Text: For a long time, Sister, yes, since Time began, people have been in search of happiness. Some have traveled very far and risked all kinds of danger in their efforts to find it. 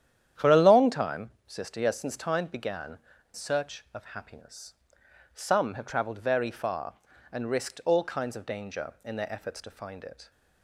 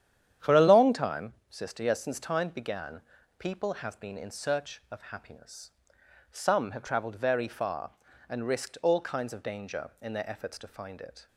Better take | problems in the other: second | starts louder than the rest; strong; until 1.5 s; 10 dB; strong in the second // skips "people have been in"; at 3.1 s

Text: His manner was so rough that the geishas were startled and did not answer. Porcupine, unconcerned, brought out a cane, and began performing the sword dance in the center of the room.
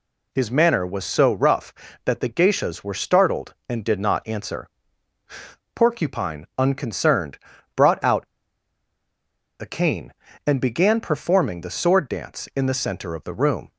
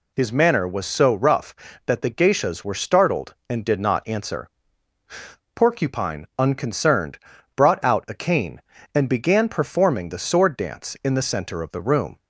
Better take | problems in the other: second | pauses between "out" and "a"; strong; at 8.2 s; 1.3 s long

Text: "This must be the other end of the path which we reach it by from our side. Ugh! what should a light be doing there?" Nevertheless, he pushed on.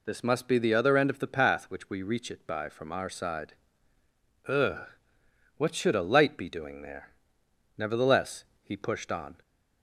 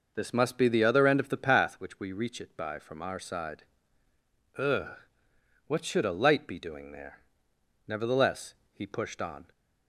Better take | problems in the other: first | starts louder than the rest; noticeable; until 1.7 s; 5.5 dB

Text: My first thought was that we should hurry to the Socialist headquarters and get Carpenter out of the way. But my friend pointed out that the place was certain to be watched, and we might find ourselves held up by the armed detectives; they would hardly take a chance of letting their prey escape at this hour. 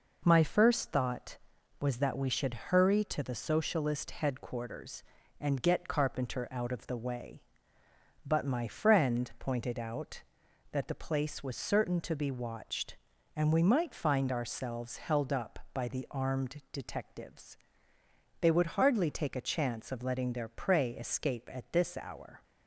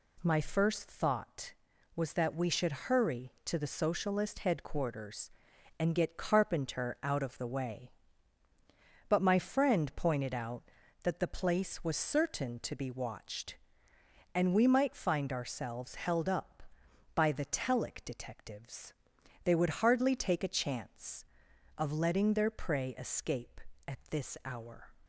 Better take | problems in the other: first | says "telic" for "armed"; at 17.4 s

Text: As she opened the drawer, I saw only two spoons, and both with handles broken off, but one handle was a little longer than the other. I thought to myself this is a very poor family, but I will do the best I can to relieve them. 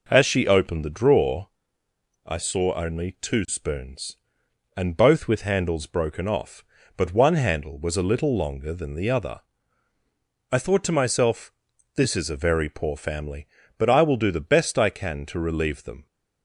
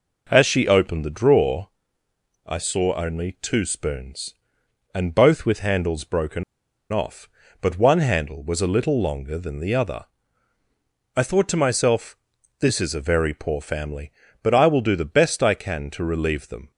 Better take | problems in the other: first | pauses between "broken" and "off"; noticeable; at 6.4 s; 0.49 s long // pauses between "myself" and "this"; at 12.1 s; 0.44 s long; also in the first

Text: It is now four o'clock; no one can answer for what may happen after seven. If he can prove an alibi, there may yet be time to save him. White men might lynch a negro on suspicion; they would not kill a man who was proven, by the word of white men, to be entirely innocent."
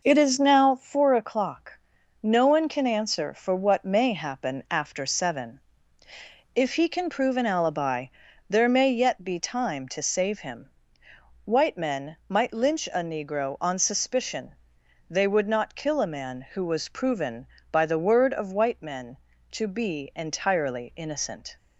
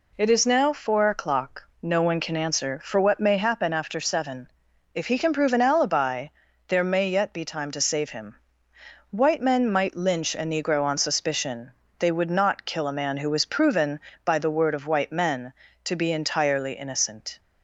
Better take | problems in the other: second | starts louder than the rest; noticeable; until 1.1 s; 5.5 dB

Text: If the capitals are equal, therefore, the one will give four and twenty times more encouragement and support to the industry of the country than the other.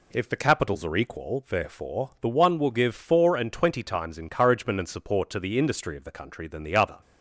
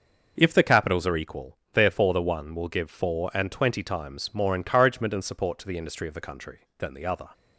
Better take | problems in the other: second | skips "more"; at 4.1 s

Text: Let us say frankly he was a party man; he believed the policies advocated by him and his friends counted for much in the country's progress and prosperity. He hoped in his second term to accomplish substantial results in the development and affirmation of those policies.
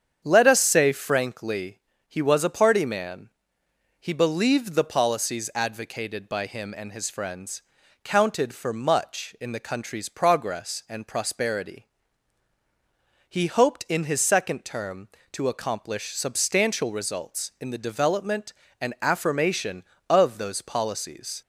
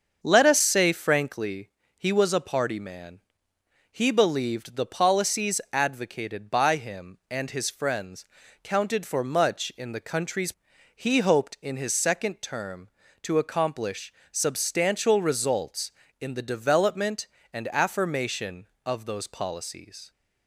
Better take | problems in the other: first | starts louder than the rest; until 1.2 s; 7 dB; strong in the first // pauses between "frankly" and "he"; slight; at 1.6 s; 0.28 s long; slight in the first // pauses between "friends" and "counted"; at 8.2 s; 0.40 s long; also in the first // skips "progress and prosperity"; at 10.7 s // pauses between "accomplish" and "substantial"; slight; at 14.1 s; 0.18 s long

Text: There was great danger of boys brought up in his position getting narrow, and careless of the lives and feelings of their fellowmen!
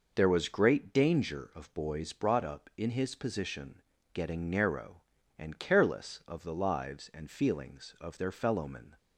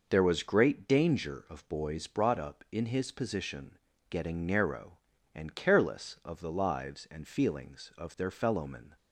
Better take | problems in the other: neither | pauses between "position" and "getting"; slight; the same in both

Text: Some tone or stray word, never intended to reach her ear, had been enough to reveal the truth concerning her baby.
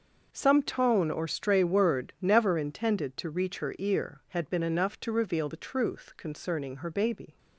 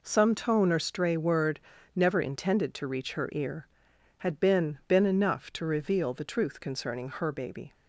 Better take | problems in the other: first | says "been" twice; at 4.8 s

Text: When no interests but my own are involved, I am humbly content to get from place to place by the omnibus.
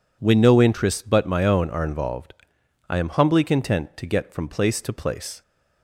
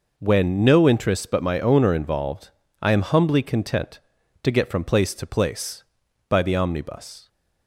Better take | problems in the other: second | stops before "by the omnibus"; at 5.4 s

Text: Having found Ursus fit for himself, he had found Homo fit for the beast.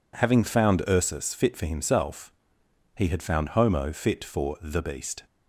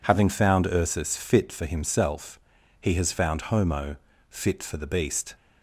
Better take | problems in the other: first | says "has" for "had"; at 2.9 s // pauses between "Homo" and "fit"; slight; at 3.9 s; 0.34 s long

